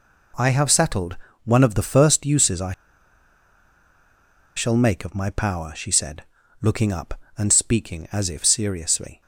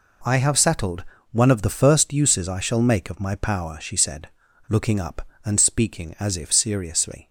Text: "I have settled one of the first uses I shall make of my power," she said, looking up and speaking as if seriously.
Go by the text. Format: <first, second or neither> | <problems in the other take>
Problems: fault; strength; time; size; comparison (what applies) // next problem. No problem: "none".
second | pauses between "settled" and "one"; slight; at 1.1 s; 0.28 s long; slight in the second // pauses between "I" and "shall"; strong; at 2.7 s; 1.8 s long